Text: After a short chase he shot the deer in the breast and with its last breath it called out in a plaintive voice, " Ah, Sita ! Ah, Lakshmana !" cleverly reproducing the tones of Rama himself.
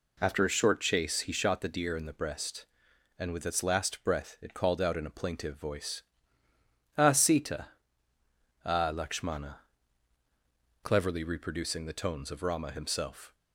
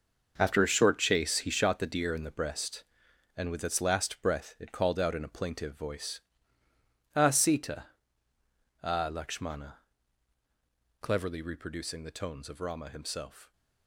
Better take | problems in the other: first | gets quieter; strong; throughout; 11.5 dB

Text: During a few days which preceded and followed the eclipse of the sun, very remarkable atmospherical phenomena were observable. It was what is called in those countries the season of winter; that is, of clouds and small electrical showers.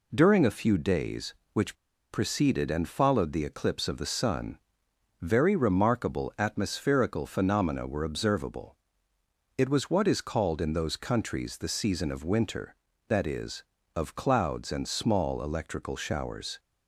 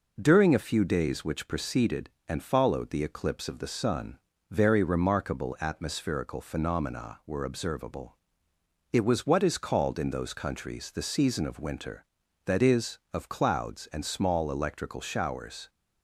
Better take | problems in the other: second | pauses between "which" and "preceded"; slight; at 1.7 s; 0.35 s long

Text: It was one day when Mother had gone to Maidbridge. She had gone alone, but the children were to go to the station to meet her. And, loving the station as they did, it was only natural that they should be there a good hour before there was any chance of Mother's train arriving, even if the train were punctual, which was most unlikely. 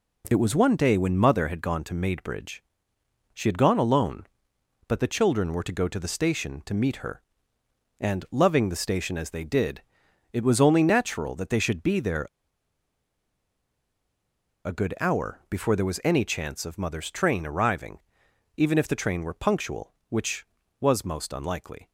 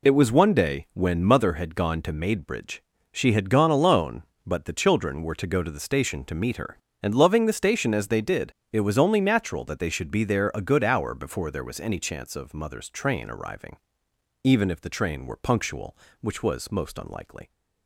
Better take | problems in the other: second | pauses between "there" and "a"; strong; at 12.2 s; 2.3 s long

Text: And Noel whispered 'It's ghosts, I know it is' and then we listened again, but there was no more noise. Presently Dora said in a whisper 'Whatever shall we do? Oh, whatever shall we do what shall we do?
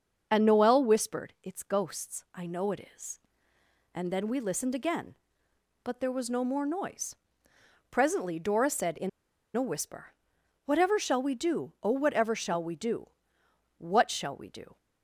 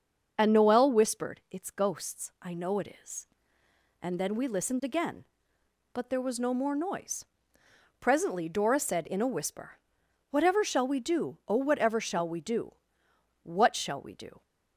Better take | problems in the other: second | starts louder than the rest; until 1.3 s; 6.5 dB; also in the second // pauses between "in" and "a"; noticeable; at 9.0 s; 0.46 s long // pauses between "whisper" and "Whatever"; noticeable; at 10.1 s; 0.54 s long; noticeable in the second // pauses between "do" and "what"; noticeable; at 13.0 s; 0.70 s long; noticeable in the second

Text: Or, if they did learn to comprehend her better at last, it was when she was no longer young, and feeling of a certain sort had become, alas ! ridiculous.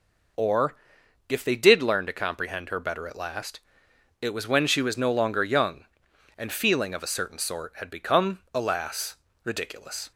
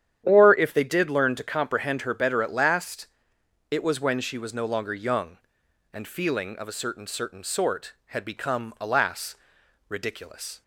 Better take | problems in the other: first | starts louder than the rest; strong; until 1.2 s; 9.5 dB // says "certain" twice; at 7.0 s

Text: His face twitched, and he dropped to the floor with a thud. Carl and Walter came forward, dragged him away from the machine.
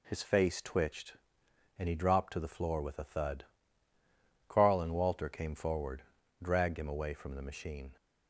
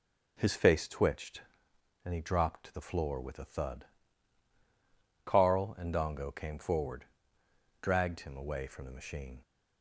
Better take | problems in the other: first | says "Dongo" for "Walter"; at 5.9 s

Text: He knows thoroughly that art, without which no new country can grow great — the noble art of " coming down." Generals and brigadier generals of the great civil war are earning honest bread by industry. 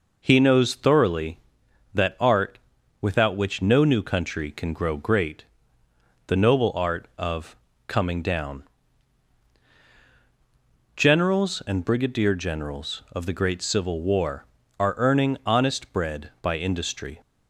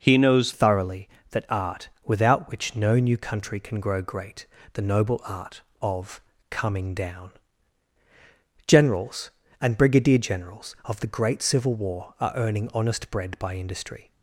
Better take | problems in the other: first | changes voice at "thoroughly"; from 0.5 s on; 13.6 s long

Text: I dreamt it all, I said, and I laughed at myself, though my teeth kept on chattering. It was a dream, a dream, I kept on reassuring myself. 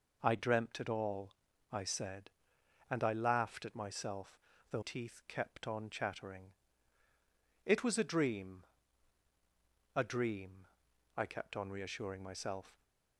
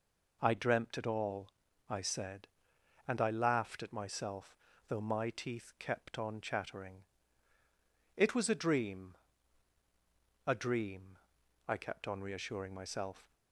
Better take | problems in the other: second | skips "my"; at 4.8 s

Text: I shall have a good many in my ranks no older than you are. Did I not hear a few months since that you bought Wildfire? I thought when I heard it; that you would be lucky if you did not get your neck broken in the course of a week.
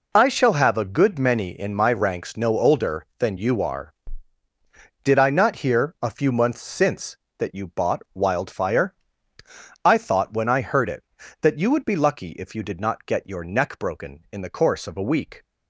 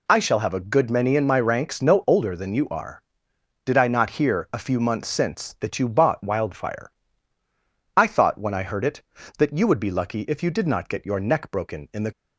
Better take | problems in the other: first | stops before "course of a week"; at 12.1 s

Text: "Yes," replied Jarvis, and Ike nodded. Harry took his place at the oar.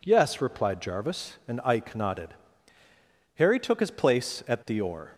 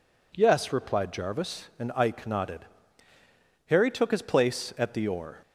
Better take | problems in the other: neither | none

